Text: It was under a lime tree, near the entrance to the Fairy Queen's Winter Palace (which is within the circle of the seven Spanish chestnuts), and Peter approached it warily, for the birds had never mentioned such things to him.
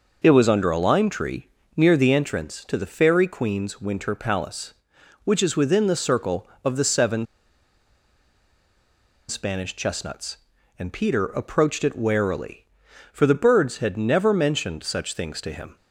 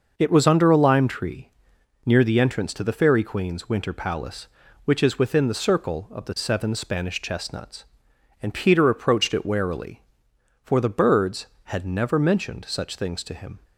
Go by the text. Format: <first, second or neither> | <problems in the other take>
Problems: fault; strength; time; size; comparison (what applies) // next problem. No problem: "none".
second | pauses between "seven" and "Spanish"; strong; at 7.2 s; 2.0 s long